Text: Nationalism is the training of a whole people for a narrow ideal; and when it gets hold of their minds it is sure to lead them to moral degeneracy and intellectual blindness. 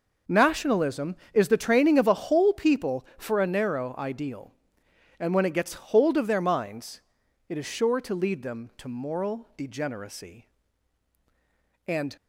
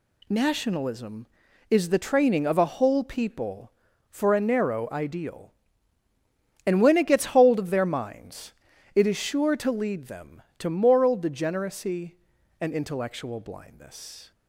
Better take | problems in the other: second | pauses between "minds" and "it"; noticeable; at 7.0 s; 0.48 s long; also in the second // stops before "intellectual blindness"; at 12.1 s

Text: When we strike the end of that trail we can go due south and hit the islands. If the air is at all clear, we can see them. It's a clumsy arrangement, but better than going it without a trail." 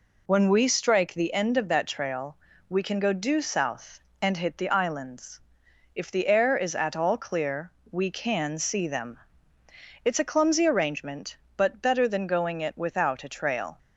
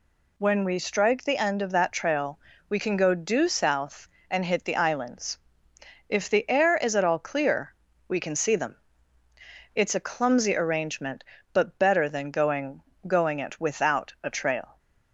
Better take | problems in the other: first | pauses between "trail" and "we"; slight; at 2.3 s; 0.32 s long; slight in the first // says "going" twice; at 13.0 s

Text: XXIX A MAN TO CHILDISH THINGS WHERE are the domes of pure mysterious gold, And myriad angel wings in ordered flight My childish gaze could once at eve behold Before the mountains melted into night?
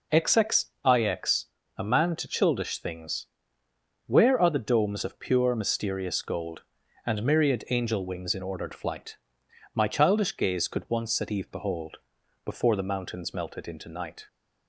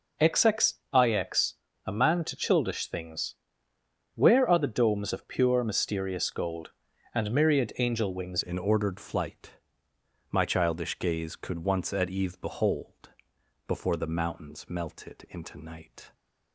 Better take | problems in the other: first | pauses between "XXIX" and "A"; slight; at 1.5 s; 0.32 s long; slight in the first // pauses between "THINGS" and "WHERE"; noticeable; at 3.3 s; 0.80 s long; noticeable in the first // changes voice at "in"; from 8.4 s on; 7.7 s long // pauses between "flight" and "My"; noticeable; at 9.5 s; 0.76 s long; noticeable in the first // pauses between "behold" and "Before"; noticeable; at 13.0 s; 0.58 s long; also in the first

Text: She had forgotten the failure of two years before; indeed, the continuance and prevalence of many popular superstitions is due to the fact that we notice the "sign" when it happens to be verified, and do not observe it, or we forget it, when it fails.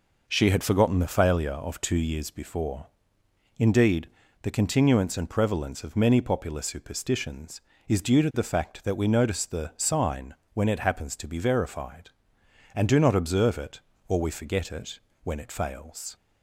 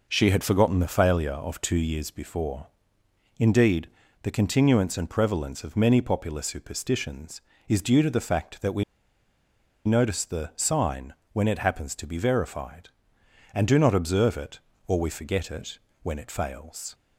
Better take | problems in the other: first | pauses between "we" and "notice"; at 8.8 s; 1.0 s long // pauses between "sign" and "when"; slight; at 11.1 s; 0.18 s long; slight in the first

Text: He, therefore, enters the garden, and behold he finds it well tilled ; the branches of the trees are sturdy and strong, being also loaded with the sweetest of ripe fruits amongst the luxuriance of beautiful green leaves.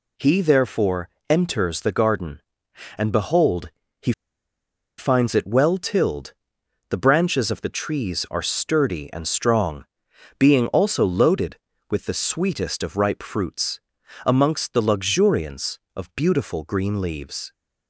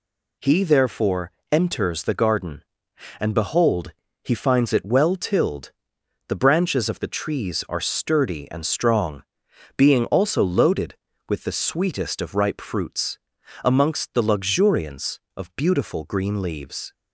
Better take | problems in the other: second | pauses between "behold" and "he"; slight; at 3.6 s; 0.30 s long; slight in the second // pauses between "he" and "finds"; noticeable; at 4.1 s; 0.86 s long // pauses between "fruits" and "amongst"; noticeable; at 13.7 s; 0.46 s long; noticeable in the second

